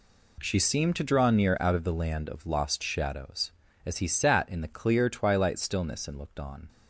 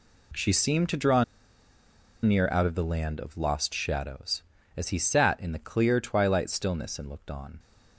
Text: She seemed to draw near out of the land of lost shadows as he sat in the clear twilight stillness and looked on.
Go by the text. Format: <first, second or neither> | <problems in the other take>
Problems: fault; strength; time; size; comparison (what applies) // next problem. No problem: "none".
first | pauses between "draw" and "near"; at 1.2 s; 0.98 s long